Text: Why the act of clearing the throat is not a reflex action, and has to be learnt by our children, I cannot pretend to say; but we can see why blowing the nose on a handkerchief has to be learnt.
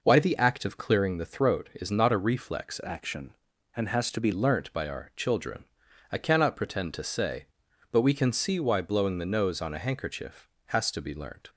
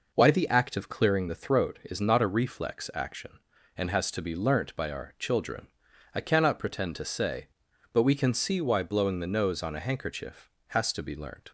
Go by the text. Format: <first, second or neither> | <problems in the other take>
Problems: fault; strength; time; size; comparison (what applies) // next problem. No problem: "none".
second | changes voice from "action" to "be"; from 2.8 to 4.3 s; 1.5 s long